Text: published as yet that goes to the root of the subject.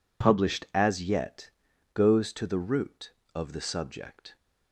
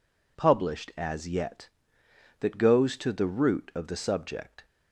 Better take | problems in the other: second | skips "that"; at 1.7 s

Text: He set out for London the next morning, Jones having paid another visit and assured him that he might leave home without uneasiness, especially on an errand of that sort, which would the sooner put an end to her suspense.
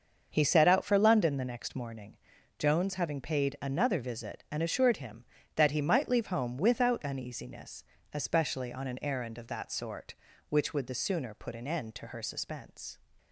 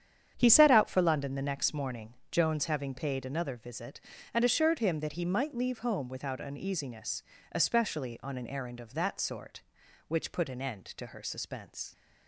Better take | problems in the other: first | starts louder than the rest; strong; until 1.3 s; 8.5 dB; also in the first // skips "would the sooner"; at 10.3 s

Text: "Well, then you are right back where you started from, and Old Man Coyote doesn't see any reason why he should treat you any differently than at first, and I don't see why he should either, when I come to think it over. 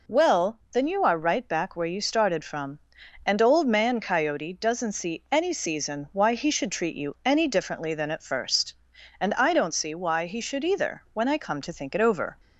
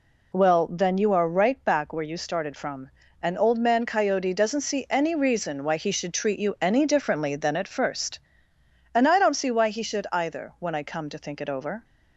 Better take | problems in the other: second | says "season" for "reason"; at 5.5 s

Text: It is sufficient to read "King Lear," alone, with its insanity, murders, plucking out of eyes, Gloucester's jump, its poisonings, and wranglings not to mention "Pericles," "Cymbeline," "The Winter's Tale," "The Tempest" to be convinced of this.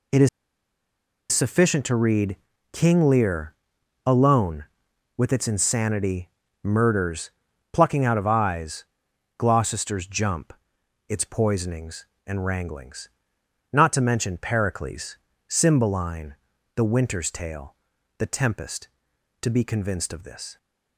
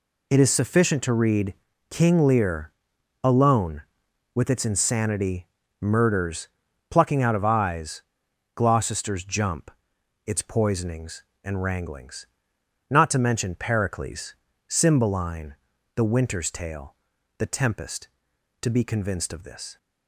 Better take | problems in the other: second | pauses between "is" and "sufficient"; at 0.2 s; 1.0 s long // pauses between "read" and "King"; at 2.3 s; 0.38 s long; also in the second // pauses between "wranglings" and "not"; noticeable; at 13.0 s; 0.64 s long; noticeable in the second

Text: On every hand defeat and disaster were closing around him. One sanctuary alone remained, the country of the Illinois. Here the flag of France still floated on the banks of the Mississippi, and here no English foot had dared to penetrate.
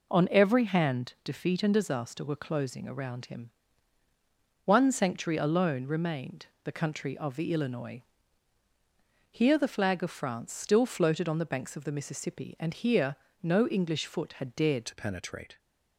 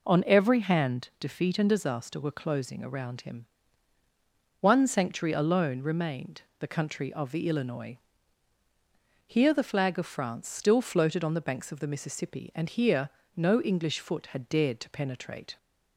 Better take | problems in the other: second | pauses between "here" and "no"; slight; at 13.1 s; 0.28 s long; slight in the second // changes voice at "to"; from 14.8 s on; 0.7 s long

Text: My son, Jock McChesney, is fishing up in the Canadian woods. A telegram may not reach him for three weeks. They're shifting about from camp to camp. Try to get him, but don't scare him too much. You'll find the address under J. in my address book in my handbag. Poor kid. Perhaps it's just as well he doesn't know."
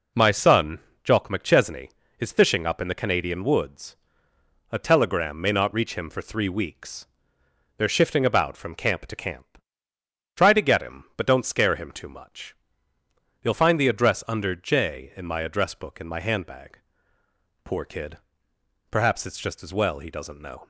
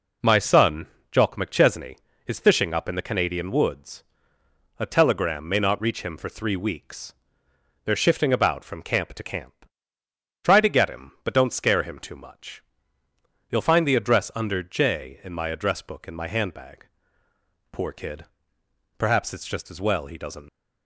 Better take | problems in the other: first | stops before "know"; at 20.4 s

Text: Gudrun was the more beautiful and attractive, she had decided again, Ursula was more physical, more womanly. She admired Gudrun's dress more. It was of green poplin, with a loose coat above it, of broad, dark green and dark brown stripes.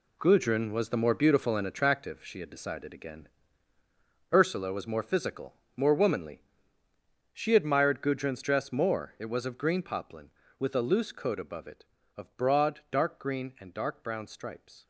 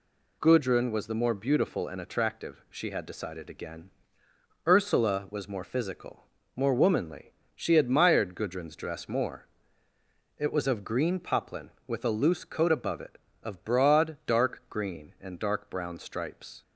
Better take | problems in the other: second | gets quieter; strong; throughout; 10 dB

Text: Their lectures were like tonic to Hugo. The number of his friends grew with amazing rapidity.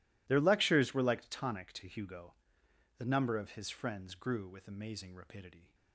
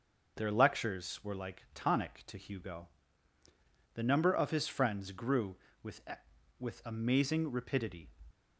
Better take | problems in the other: first | says "with" twice; at 6.5 s

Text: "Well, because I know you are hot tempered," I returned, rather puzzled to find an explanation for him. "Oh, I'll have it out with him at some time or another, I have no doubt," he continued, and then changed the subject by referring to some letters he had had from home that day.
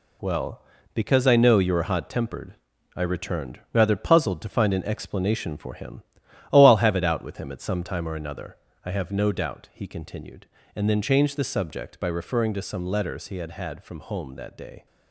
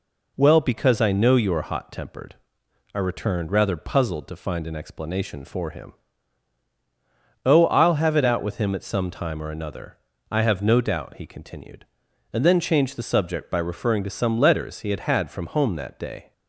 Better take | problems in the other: second | gets quieter; strong; throughout; 7.5 dB

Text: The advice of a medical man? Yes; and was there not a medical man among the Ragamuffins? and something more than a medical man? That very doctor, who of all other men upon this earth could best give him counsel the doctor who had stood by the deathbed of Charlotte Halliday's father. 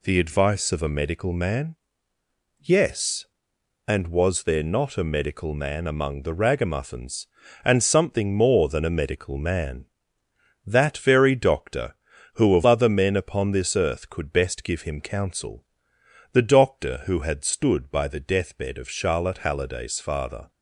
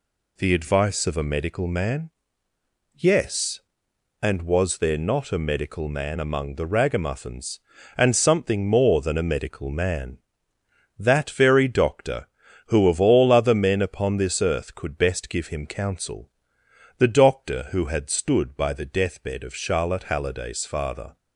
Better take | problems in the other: second | skips "all"; at 12.6 s // pauses between "counsel" and "the"; noticeable; at 15.6 s; 0.68 s long; noticeable in the second

